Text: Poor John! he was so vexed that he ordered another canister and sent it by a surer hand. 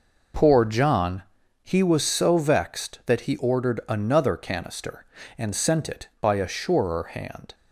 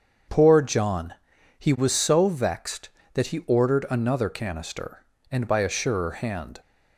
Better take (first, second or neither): first